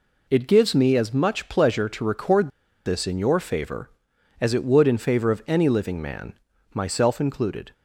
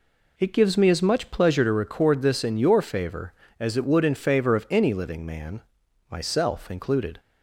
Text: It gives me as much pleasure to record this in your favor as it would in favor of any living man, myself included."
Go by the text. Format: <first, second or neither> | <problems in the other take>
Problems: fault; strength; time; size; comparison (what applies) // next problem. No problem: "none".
second | pauses between "record" and "this"; at 2.4 s; 0.36 s long